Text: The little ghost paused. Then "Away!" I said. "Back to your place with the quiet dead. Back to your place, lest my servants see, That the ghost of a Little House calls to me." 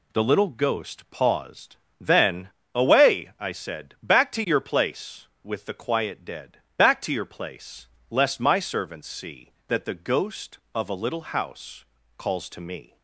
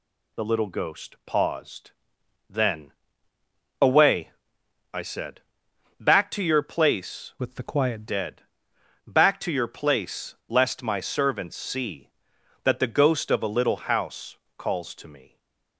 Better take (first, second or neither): first